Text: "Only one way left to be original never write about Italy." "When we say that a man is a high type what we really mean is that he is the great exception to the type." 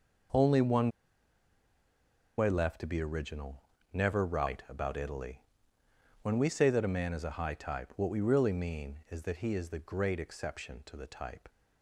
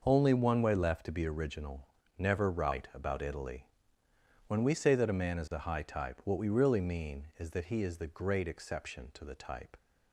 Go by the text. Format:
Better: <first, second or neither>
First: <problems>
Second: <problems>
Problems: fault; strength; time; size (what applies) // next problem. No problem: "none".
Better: second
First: pauses between "one" and "way"; strong; at 0.8 s; 1.4 s long // pauses between "original" and "never"; slight; at 3.6 s; 0.32 s long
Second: pauses between "original" and "never"; slight; at 1.8 s; 0.32 s long